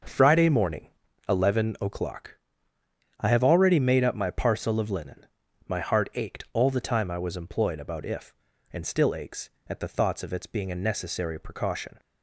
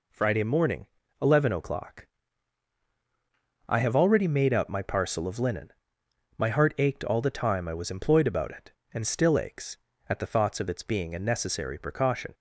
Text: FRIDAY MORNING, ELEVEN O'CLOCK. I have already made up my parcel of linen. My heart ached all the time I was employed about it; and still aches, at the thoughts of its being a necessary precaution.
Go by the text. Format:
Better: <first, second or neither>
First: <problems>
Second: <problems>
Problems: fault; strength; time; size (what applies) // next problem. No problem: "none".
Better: second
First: starts louder than the rest; until 1.4 s; 6 dB // says "if" for "it"; at 8.0 s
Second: none